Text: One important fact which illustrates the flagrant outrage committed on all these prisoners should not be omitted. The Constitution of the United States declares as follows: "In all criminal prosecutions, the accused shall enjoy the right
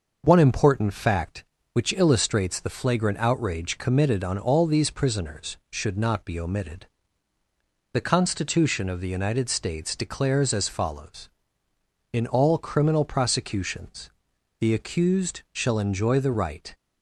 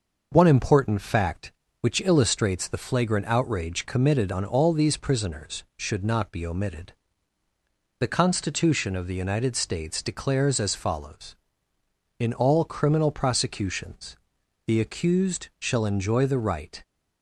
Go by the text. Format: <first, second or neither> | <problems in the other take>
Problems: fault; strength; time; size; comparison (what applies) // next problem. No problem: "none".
neither | starts louder than the rest; noticeable; the same in both